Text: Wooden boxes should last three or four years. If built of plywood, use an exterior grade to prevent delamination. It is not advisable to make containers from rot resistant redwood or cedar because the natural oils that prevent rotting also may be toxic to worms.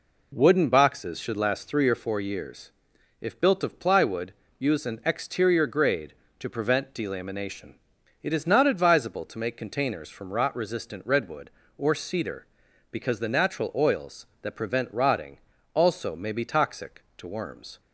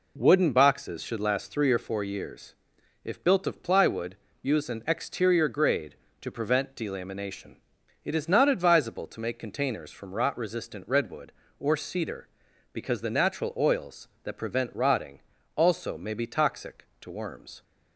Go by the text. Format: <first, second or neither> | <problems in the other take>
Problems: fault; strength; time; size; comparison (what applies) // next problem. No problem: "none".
neither | pauses between "rotting" and "also"; the same in both